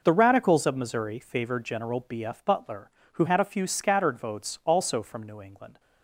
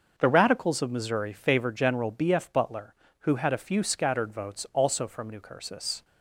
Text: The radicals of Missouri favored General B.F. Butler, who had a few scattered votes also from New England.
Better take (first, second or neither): first